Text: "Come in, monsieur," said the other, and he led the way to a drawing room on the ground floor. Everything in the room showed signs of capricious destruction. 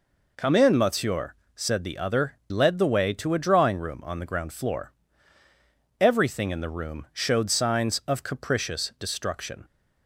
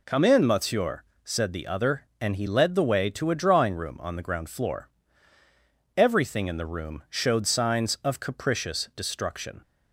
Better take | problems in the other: second | skips "and he"; at 2.4 s

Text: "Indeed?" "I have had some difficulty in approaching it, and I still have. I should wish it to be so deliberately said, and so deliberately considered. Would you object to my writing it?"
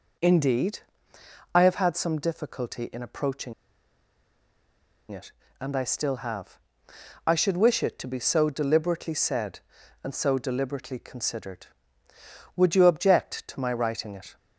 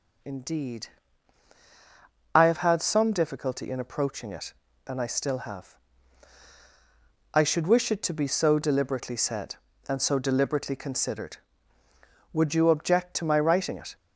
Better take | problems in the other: second | pauses between "approaching" and "it"; strong; at 3.5 s; 1.5 s long

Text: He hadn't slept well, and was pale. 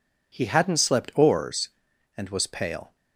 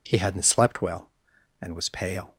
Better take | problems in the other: second | says "oars" for "well"; at 1.1 s

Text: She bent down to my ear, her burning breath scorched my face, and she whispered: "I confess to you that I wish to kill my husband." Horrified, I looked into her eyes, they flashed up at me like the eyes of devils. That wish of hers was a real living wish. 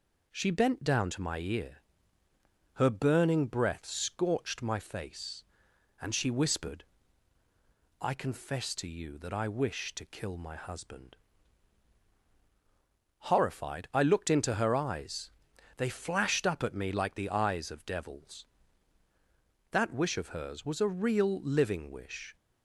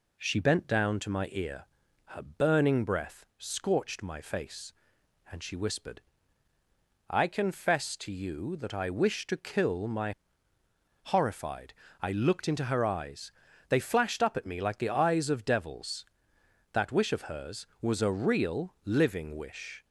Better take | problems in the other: first | skips "husband"; at 10.5 s

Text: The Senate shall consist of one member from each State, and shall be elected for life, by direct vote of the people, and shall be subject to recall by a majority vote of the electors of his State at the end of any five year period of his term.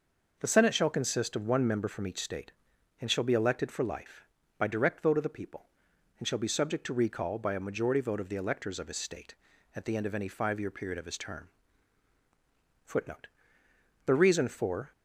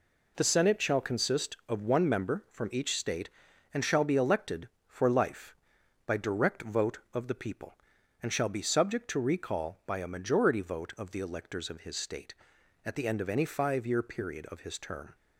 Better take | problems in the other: second | goes on to say "Footnote The reason for"; strong; from 12.8 s on; 2.0 s long

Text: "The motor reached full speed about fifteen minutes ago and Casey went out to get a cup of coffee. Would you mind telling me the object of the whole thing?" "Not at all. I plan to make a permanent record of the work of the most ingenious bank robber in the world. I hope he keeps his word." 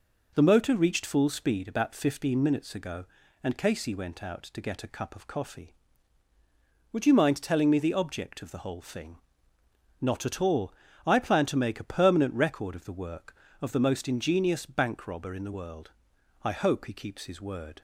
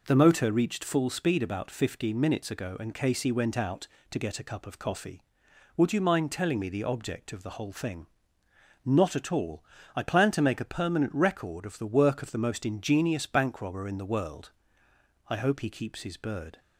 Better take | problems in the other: first | says "bird" for "word"; at 16.1 s

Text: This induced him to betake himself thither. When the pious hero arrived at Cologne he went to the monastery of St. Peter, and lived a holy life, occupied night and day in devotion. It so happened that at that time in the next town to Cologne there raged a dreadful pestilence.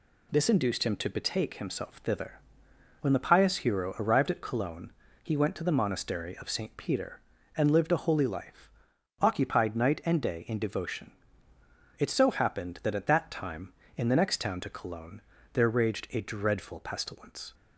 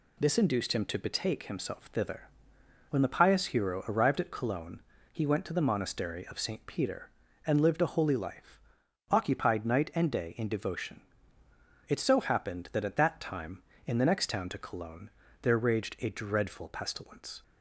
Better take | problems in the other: neither | pauses between "Cologne" and "he"; slight; the same in both // pauses between "Cologne" and "there"; slight; the same in both

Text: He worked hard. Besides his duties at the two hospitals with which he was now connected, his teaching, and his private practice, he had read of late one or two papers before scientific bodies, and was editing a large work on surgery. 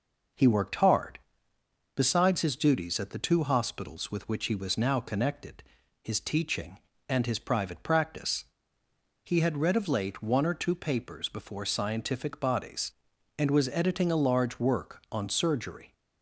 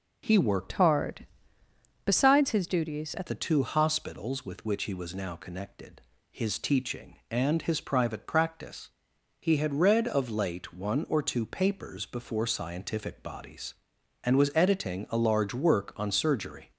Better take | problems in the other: first | changes voice from "hard" to "at"; from 0.7 to 3.2 s; 2.5 s long

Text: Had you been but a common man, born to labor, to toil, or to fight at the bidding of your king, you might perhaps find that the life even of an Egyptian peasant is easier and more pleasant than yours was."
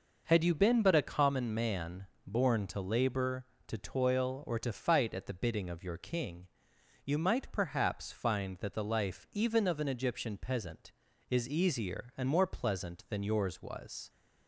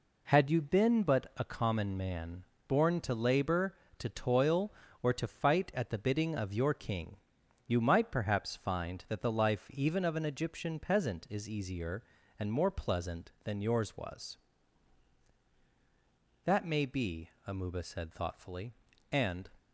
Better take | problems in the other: first | goes on to say "That may be Amuba said thoughtfully and"; strong; from 16.4 s on; 3.0 s long

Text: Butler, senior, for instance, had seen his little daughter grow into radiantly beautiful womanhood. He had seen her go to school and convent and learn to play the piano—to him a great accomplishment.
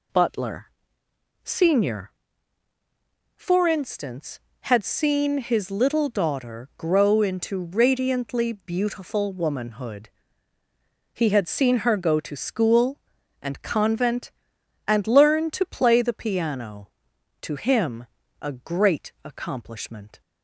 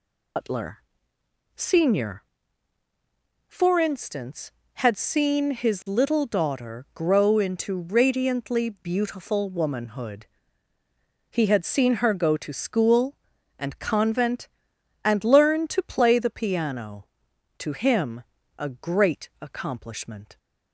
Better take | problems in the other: first | loses the start of "Butler"; at 0.3 s; 125 ms // pauses between "him" and "a"; slight; at 18.2 s; 0.34 s long; slight in the first

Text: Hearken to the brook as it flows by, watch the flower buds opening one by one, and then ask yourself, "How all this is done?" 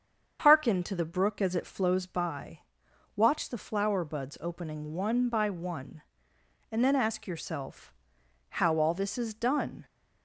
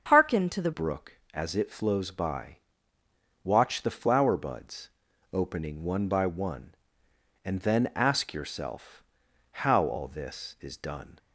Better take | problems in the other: first | starts louder than the rest; until 1.1 s; 7 dB; also in the first // changes voice at "brook"; from 0.7 s on; 10.4 s long // pauses between "buds" and "opening"; at 4.8 s; 0.44 s long

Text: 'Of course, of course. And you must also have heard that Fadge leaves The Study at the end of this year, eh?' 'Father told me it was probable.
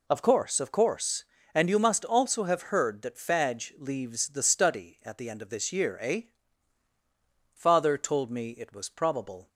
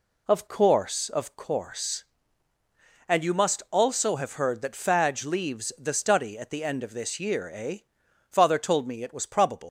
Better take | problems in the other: first | leaves "probable" unfinished; at 9.6 s; 115 ms

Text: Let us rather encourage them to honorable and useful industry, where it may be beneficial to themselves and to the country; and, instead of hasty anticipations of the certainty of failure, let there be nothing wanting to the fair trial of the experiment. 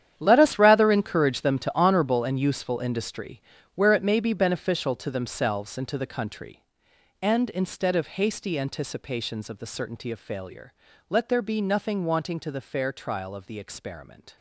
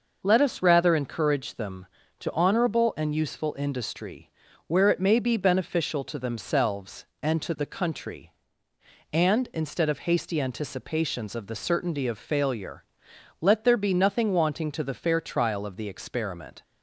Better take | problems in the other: second | gets quieter; strong; throughout; 13.5 dB

